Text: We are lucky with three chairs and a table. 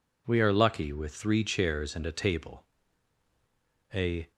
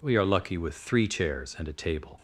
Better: second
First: goes on to say "A"; slight; from 3.9 s on; 0.38 s long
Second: none

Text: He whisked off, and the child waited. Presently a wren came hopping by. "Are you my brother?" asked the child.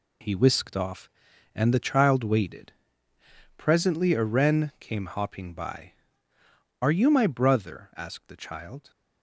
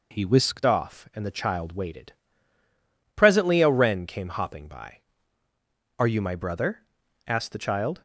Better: first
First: none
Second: changes voice at "off"; from 0.6 s on; 7.4 s long

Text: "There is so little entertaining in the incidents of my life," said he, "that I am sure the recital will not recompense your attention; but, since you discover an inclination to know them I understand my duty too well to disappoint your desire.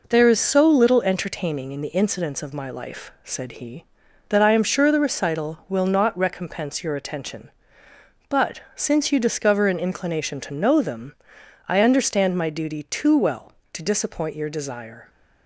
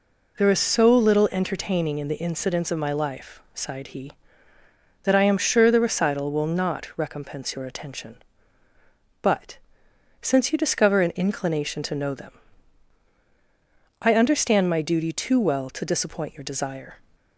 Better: first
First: pauses between "them" and "I"; noticeable; at 11.1 s; 0.52 s long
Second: says "sighed" for "said"; at 3.5 s // pauses between "them" and "I"; strong; at 12.3 s; 1.7 s long

